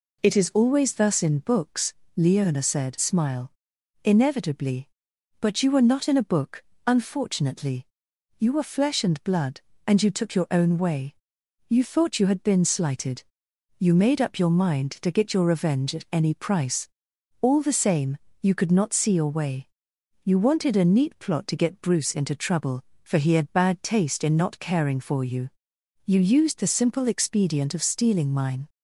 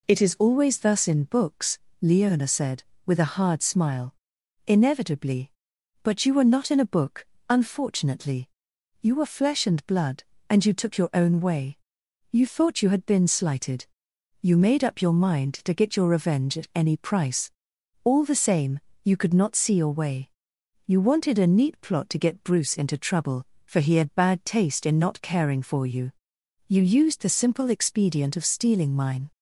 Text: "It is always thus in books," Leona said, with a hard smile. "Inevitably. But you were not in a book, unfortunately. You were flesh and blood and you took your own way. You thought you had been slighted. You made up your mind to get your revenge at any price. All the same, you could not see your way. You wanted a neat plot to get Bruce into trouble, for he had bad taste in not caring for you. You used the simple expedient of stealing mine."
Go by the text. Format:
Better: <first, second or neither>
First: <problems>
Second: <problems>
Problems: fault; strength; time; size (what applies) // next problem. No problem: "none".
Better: second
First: skips "with a hard"; at 2.9 s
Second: none